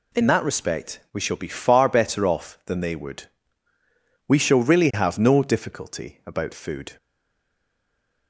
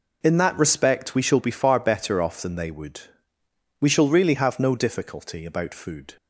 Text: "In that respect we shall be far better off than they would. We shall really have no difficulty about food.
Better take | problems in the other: second | stays silent after the last word; noticeable; from 6.9 s on; 1.3 s long

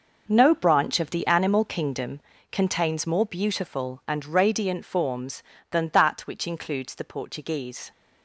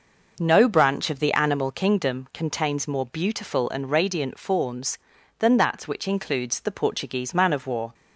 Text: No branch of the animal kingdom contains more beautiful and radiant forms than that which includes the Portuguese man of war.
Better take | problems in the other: second | pauses between "kingdom" and "contains"; slight; at 2.1 s; 0.32 s long // stops before "man of war"; at 7.9 s

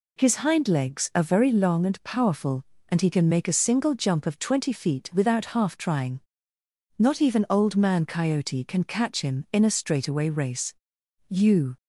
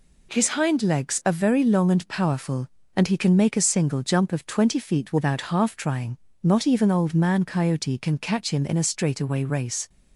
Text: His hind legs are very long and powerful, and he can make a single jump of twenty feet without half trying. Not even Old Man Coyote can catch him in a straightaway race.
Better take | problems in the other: second | goes on to say "You"; slight; from 11.2 s on; 0.48 s long

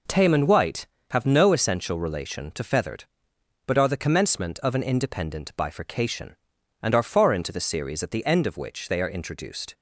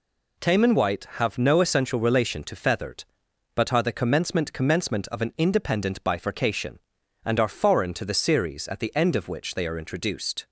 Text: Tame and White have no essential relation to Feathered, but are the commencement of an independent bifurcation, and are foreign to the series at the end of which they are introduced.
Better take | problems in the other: first | says "commencement" twice; at 4.5 s

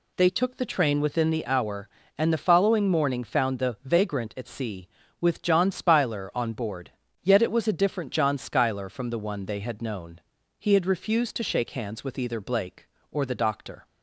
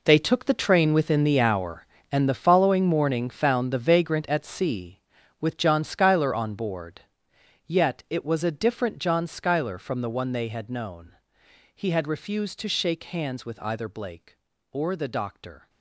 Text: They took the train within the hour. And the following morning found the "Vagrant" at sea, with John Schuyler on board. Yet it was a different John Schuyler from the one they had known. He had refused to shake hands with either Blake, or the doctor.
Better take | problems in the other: first | gets quieter; strong; throughout; 13.5 dB

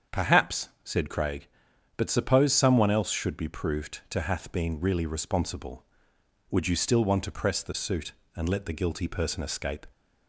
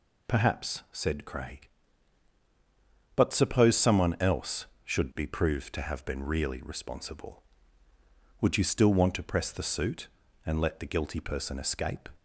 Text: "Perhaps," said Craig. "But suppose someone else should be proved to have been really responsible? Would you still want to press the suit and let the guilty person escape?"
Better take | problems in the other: second | starts louder than the rest; strong; until 1.2 s; 7.5 dB // says "hath" for "have"; at 4.2 s

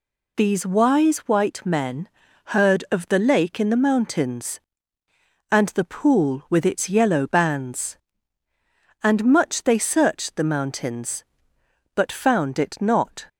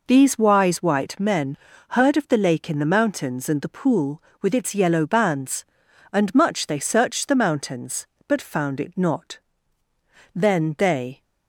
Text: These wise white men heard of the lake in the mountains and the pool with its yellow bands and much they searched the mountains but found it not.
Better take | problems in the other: first | pauses between "men" and "heard"; slight; at 1.5 s; 0.34 s long; also in the first // goes on to say "Then they"; noticeable; from 10.3 s on; 0.88 s long

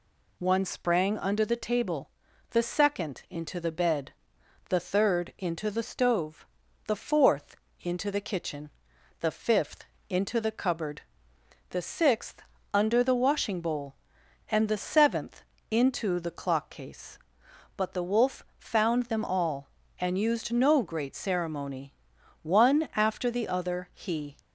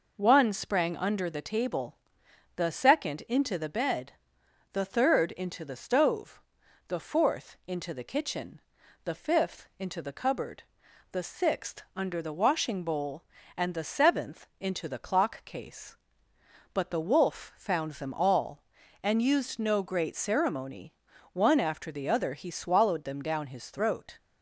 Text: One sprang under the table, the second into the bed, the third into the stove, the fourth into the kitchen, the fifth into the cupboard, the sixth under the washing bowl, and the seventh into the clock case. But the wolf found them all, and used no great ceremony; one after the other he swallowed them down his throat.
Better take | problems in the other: second | pauses between "fourth" and "into"; slight; at 7.5 s; 0.26 s long // pauses between "fifth" and "into"; slight; at 9.8 s; 0.24 s long // pauses between "sixth" and "under"; slight; at 12.4 s; 0.30 s long // pauses between "seventh" and "into"; slight; at 15.4 s; 0.30 s long // pauses between "wolf" and "found"; slight; at 18.4 s; 0.16 s long // stops before "swallowed them down his throat"; at 24.3 s

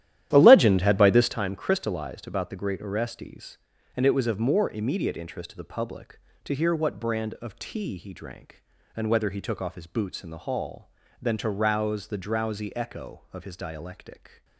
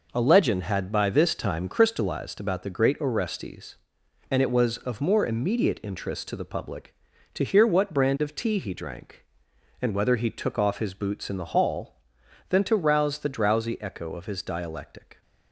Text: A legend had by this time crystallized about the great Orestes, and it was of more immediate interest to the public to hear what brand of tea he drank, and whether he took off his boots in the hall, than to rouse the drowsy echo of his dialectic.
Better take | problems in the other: second | starts louder than the rest; strong; until 1.4 s; 12 dB

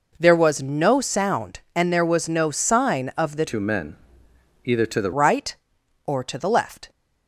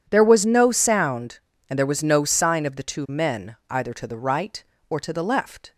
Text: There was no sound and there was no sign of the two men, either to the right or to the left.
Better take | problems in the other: second | changes voice from "two" to "the"; from 3.4 to 5.1 s; 1.7 s long

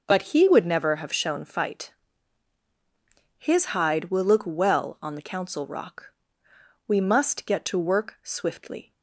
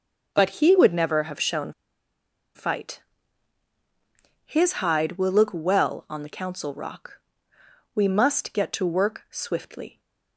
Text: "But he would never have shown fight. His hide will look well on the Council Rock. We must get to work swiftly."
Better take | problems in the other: first | pauses between "shown" and "fight"; noticeable; at 1.7 s; 0.83 s long

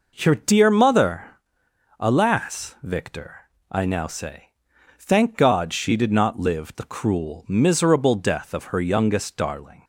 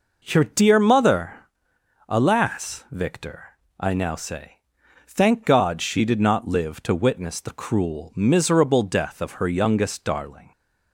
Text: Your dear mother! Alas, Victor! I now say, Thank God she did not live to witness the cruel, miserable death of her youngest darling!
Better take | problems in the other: second | skips "to witness"; at 6.7 s

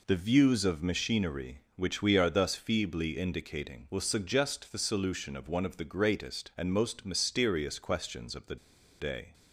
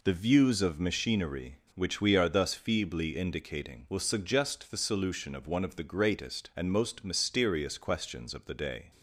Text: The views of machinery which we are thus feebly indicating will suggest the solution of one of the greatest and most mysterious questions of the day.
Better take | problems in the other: second | pauses between "the" and "day"; at 8.5 s; 0.44 s long

